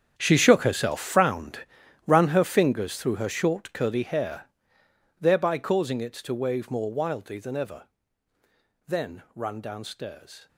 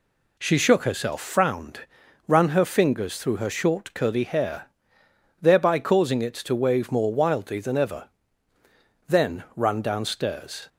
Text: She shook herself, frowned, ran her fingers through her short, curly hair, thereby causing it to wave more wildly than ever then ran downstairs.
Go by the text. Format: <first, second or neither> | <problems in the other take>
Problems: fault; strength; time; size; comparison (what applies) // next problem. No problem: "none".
second | gets quieter; strong; throughout; 16 dB // pauses between "ever" and "then"; at 7.8 s; 1.0 s long; also in the second